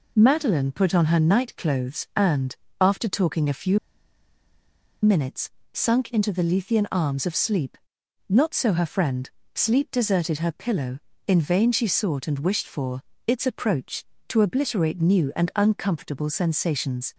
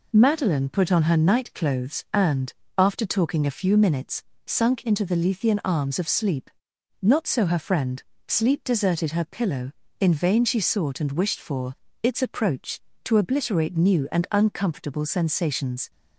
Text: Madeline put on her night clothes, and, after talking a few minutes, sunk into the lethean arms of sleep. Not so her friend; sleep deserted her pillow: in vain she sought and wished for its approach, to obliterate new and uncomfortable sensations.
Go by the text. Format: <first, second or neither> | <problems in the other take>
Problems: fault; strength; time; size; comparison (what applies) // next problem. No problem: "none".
second | pauses between "few" and "minutes"; at 3.7 s; 1.2 s long // pauses between "for" and "its"; slight; at 13.0 s; 0.26 s long; slight in the second